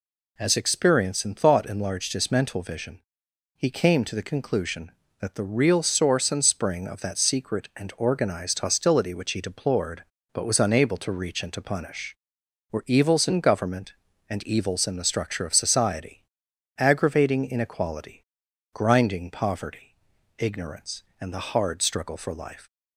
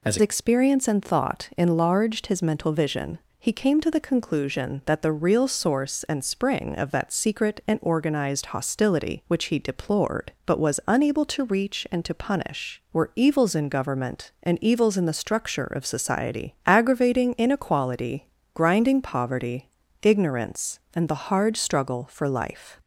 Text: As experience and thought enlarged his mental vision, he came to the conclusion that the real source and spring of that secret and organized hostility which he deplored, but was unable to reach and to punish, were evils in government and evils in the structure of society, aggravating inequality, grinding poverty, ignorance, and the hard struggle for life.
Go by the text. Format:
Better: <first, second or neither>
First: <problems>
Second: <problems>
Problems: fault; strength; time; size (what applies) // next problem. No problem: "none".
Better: first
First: none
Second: changes voice at "experience"; from 0.2 s on; 22.5 s long